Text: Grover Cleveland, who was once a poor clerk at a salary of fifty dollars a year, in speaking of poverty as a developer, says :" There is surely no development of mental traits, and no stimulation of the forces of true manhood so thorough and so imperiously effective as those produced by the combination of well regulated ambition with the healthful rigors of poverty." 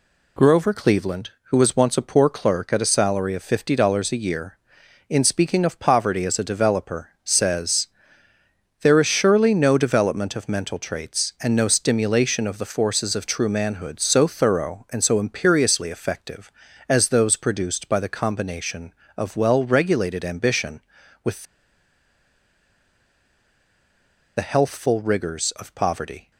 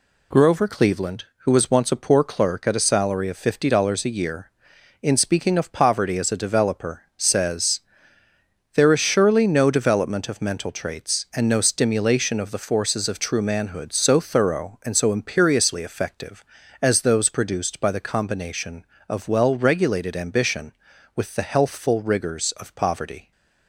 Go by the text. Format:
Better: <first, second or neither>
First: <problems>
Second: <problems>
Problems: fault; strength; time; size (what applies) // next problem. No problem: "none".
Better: second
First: pauses between "with" and "the"; strong; at 21.4 s; 2.9 s long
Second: none